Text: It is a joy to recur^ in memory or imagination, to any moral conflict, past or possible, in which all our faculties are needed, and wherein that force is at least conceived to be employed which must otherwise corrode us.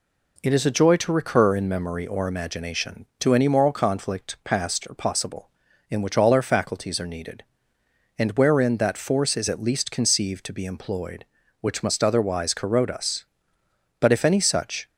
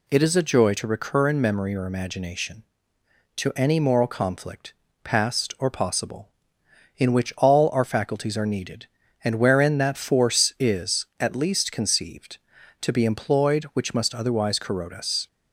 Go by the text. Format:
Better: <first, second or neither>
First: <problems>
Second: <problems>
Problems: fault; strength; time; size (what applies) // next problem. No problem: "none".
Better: second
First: goes on to say "But if any such"; noticeable; from 14.0 s on; 0.88 s long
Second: none